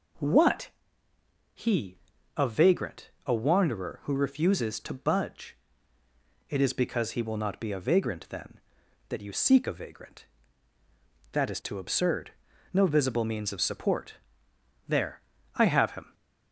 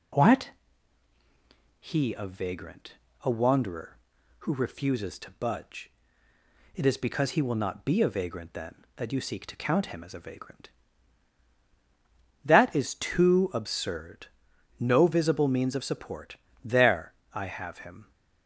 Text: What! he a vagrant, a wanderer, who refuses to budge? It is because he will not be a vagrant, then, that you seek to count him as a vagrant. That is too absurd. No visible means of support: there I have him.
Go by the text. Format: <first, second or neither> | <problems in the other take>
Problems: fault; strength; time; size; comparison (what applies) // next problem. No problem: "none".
second | pauses between "he" and "a"; at 1.9 s; 0.40 s long // skips "to count him as"; at 9.6 s // pauses between "there" and "I"; slight; at 15.2 s; 0.34 s long; slight in the second